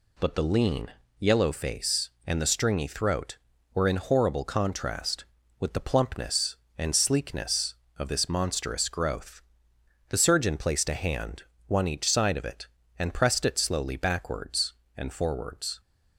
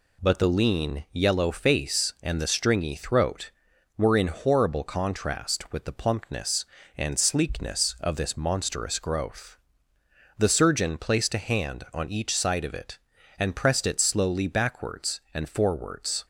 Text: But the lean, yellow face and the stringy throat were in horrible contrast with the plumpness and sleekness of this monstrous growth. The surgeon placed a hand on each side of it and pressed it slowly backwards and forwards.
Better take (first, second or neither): second